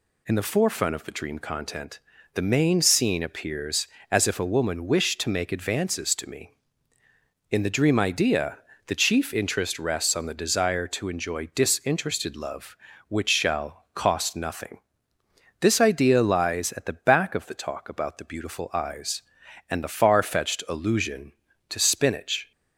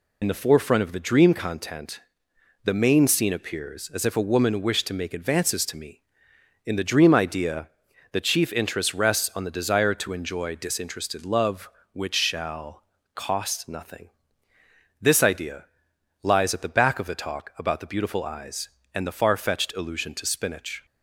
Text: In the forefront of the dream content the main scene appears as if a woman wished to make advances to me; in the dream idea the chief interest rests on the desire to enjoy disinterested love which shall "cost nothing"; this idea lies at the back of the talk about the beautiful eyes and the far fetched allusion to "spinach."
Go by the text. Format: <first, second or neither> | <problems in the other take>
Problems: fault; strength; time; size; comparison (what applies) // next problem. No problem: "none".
first | loses the start of "In"; at 0.2 s; 50 ms // pauses between "content" and "the"; noticeable; at 1.9 s; 0.64 s long; slight in the first // pauses between "idea" and "the"; noticeable; at 7.6 s; 0.46 s long; slight in the first // pauses between "shall" and "cost"; slight; at 12.8 s; 0.30 s long // pauses between "idea" and "lies"; noticeable; at 15.6 s; 0.58 s long